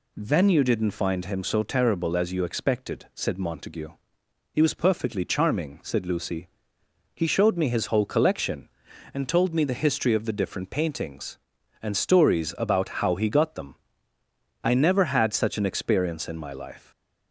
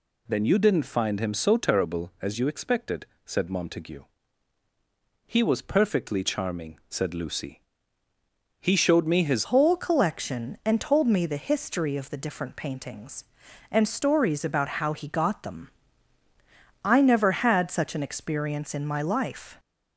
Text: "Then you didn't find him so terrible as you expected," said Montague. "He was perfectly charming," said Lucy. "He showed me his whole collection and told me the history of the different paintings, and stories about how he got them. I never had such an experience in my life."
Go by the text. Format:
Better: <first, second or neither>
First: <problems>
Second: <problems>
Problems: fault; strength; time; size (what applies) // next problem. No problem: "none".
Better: first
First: none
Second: changes voice at "whole"; from 9.4 s on; 10.1 s long